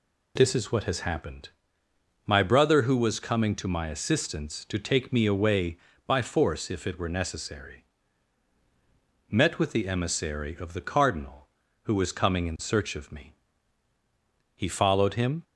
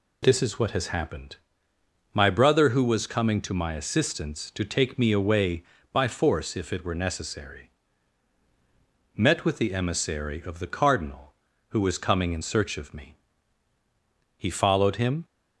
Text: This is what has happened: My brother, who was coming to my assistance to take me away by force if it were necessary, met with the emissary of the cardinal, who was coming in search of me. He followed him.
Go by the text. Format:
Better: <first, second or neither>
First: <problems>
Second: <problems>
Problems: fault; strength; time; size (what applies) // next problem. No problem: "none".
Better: neither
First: none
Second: none